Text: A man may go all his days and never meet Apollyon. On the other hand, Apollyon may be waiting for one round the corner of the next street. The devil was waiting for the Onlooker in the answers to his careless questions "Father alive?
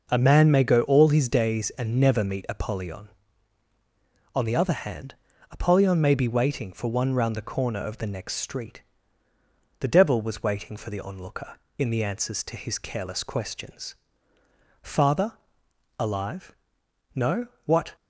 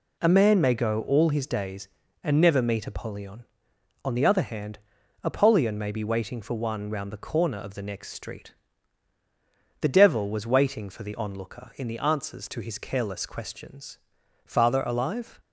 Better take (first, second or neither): second